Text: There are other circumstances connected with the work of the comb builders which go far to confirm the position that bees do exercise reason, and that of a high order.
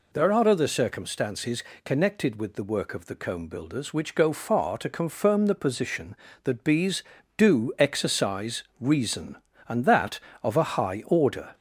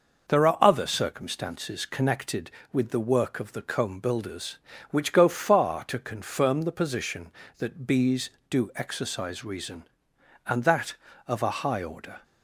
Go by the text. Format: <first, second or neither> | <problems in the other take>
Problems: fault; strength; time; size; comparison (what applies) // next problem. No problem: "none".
second | gets louder; slight; throughout; 2.5 dB // pauses between "circumstances" and "connected"; slight; at 1.6 s; 0.24 s long // pauses between "exercise" and "reason"; slight; at 8.6 s; 0.16 s long